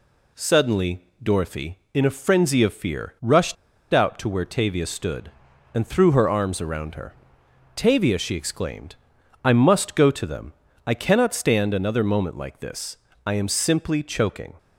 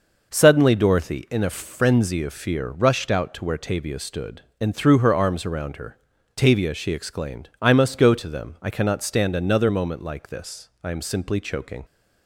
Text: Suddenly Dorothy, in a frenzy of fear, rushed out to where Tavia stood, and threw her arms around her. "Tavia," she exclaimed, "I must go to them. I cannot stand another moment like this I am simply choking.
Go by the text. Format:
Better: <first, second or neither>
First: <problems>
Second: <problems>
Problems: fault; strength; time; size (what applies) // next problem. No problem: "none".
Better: second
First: pauses between "Suddenly" and "Dorothy"; slight; at 1.0 s; 0.16 s long // pauses between "rushed" and "out"; at 3.5 s; 0.37 s long // pauses between "this" and "I"; slight; at 12.9 s; 0.30 s long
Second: none